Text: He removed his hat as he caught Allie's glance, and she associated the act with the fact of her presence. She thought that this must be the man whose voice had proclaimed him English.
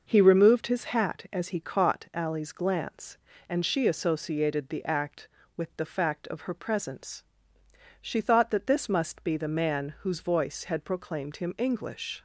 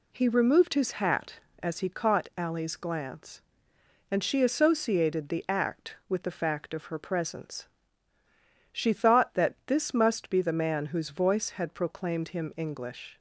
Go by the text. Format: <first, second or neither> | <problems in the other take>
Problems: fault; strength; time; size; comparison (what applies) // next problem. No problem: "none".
neither | none